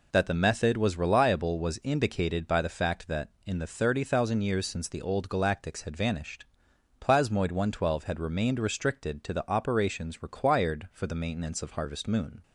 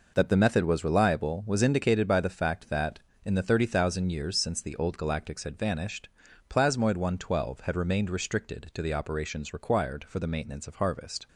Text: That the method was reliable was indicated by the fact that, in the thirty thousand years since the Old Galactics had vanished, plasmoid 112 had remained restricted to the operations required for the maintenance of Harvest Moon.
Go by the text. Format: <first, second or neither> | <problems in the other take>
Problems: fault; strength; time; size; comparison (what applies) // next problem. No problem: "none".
first | stops before "Moon"; at 11.2 s